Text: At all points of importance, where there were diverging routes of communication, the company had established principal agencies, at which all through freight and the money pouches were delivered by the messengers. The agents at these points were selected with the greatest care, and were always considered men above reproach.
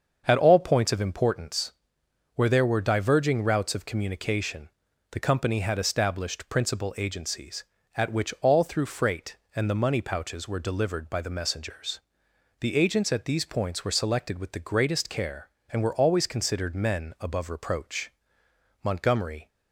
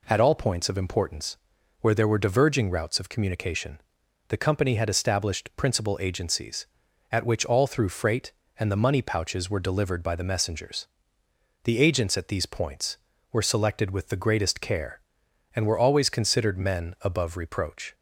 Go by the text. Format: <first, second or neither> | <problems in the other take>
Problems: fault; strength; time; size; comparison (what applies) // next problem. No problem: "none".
second | starts louder than the rest; until 1.2 s; 7 dB // goes on to say "Montgomery"; noticeable; from 18.8 s on; 0.64 s long